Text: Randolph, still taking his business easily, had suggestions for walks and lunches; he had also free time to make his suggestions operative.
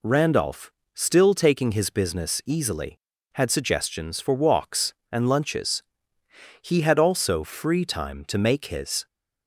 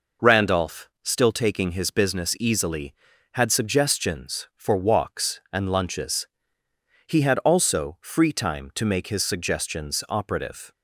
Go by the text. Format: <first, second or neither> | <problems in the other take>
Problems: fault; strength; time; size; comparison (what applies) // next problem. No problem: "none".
second | stops before "suggestions operative"; at 9.0 s